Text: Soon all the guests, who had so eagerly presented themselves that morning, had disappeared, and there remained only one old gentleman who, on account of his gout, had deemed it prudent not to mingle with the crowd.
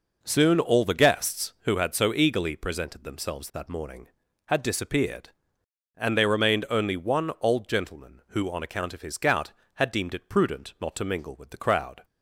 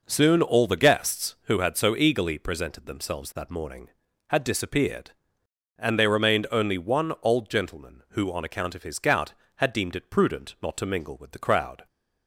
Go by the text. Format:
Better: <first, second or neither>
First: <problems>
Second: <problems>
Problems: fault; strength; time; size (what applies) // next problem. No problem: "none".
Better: neither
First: none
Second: none